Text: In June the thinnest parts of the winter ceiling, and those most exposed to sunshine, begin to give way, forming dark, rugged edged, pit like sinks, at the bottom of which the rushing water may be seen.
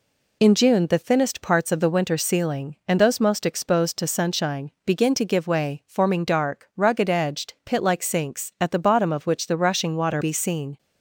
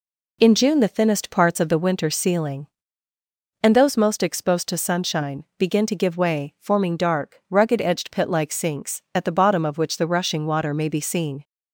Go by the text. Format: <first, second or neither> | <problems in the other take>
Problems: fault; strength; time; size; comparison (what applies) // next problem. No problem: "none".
second | skips "may"; at 10.2 s